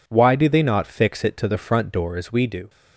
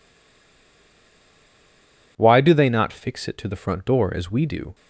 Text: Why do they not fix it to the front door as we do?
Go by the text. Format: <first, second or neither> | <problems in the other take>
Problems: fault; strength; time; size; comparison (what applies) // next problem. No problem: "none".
first | stays silent before the first word; until 2.1 s; 2.1 s long